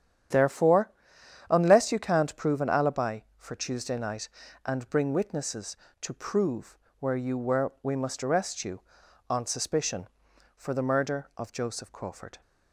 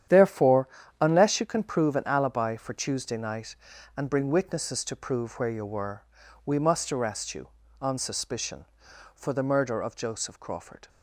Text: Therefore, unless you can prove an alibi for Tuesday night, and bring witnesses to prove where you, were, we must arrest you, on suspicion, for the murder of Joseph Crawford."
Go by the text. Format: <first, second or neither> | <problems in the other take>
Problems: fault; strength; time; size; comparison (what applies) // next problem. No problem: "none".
second | starts louder than the rest; strong; until 1.9 s; 9 dB; strong in the second // says "can't" for "can"; at 1.9 s // pauses between "prove" and "where"; slight; at 6.7 s; 0.24 s long